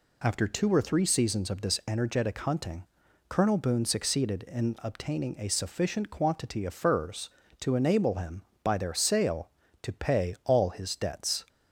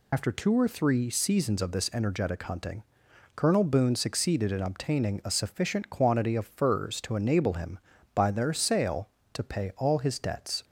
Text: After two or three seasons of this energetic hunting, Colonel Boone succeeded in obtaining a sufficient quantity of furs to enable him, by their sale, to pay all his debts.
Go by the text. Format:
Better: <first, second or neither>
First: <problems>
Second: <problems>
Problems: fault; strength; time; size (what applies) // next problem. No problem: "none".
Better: first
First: none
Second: loses the start of "After"; at 0.1 s; 65 ms